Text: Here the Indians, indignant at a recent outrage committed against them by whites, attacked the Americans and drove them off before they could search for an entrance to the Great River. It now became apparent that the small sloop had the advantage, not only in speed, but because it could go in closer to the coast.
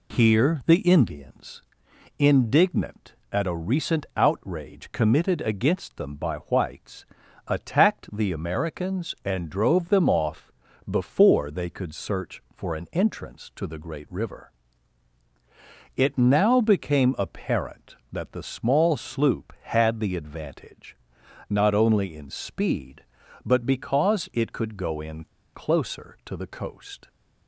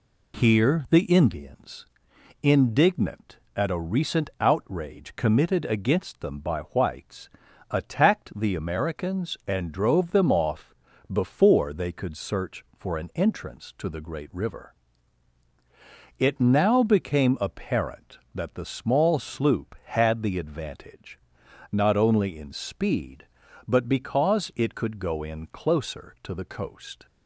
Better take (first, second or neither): second